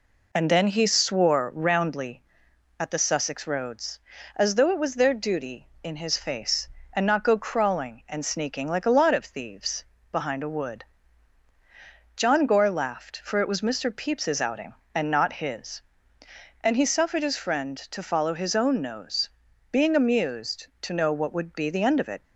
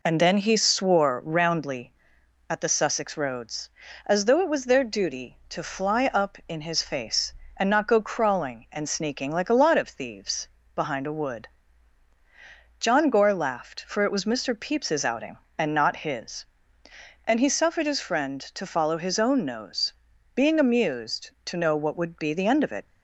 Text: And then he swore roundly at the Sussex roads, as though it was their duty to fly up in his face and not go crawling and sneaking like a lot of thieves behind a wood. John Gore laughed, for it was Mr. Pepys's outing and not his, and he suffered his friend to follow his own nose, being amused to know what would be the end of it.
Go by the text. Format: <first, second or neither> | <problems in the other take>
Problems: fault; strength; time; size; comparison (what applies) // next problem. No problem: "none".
second | skips "to fly up"; at 5.7 s // pauses between "thieves" and "behind"; slight; at 9.8 s; 0.26 s long; slight in the second